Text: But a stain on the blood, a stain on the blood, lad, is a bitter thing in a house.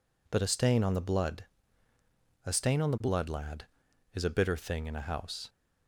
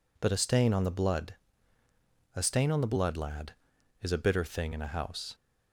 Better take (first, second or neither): neither